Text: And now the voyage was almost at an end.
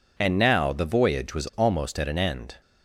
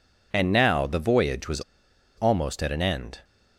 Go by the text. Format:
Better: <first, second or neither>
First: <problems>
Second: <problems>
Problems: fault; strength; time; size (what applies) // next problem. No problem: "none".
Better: first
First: none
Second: pauses between "was" and "almost"; noticeable; at 1.5 s; 0.58 s long